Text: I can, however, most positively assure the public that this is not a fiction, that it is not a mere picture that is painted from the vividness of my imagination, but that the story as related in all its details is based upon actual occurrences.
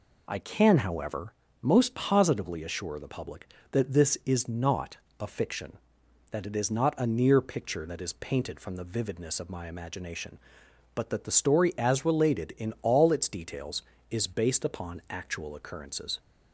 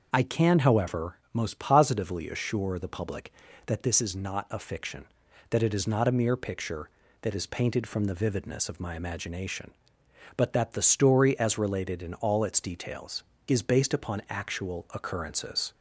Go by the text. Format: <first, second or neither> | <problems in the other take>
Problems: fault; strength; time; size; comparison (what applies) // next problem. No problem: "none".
second | pauses between "not" and "a"; slight; at 4.9 s; 0.24 s long // says "near" for "mere"; at 7.0 s